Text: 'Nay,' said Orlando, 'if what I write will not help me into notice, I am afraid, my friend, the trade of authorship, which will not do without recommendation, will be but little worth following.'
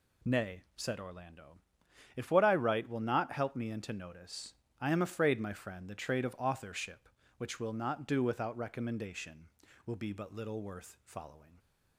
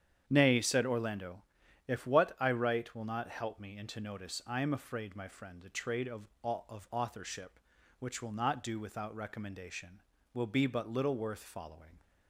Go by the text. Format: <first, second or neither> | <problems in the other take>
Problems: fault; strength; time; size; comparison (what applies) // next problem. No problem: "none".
first | starts louder than the rest; strong; until 1.2 s; 9 dB // says "of" twice; at 6.4 s